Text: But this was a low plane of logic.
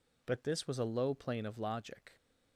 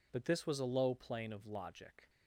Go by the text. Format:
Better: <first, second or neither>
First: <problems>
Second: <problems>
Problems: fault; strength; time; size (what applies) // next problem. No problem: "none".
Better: neither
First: none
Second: none